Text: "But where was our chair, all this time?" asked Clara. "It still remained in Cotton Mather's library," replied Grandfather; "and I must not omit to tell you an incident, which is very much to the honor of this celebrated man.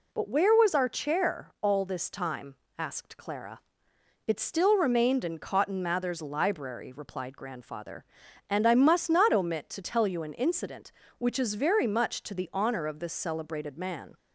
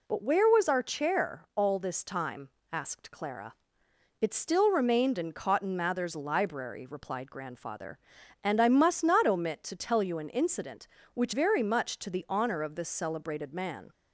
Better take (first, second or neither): first